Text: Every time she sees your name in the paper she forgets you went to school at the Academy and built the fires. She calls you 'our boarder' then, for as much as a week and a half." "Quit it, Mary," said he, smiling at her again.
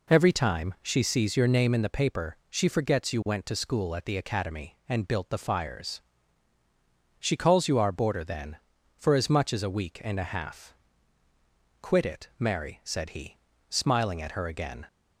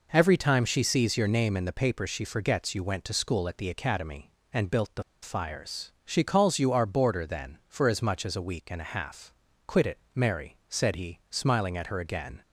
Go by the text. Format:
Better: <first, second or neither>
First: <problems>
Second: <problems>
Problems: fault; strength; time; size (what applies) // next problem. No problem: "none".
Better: first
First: none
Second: pauses between "the" and "fires"; slight; at 5.0 s; 0.20 s long